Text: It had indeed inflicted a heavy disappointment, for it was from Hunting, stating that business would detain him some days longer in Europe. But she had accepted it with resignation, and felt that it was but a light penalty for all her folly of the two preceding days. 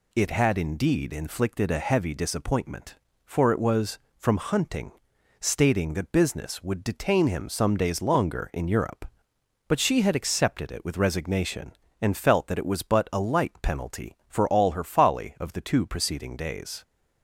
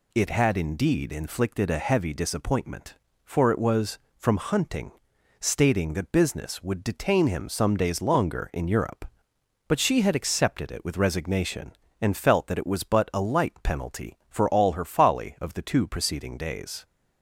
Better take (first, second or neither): neither